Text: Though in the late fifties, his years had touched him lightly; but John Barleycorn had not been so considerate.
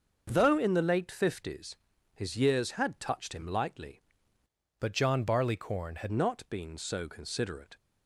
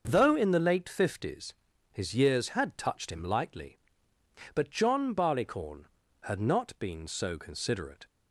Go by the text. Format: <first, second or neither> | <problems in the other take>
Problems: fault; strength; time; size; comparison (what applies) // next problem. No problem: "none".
second | starts louder than the rest; until 1.2 s; 6.5 dB; also in the second // changes voice from "but" to "had"; from 4.8 to 6.1 s; 1.3 s long